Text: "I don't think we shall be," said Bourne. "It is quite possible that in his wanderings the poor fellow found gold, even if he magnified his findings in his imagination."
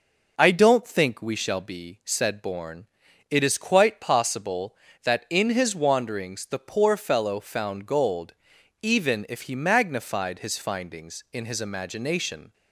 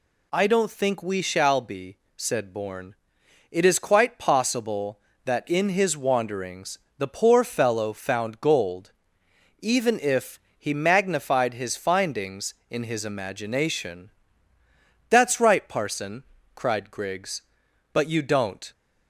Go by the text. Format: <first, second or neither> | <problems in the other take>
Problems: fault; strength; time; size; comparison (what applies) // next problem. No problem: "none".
first | pauses between "wanderings" and "the"; slight; at 6.7 s; 0.18 s long // pauses between "if" and "he"; slight; at 10.3 s; 0.18 s long // goes on to say "That's right parson cried Griggs but you don't"; strong; from 15.0 s on; 3.6 s long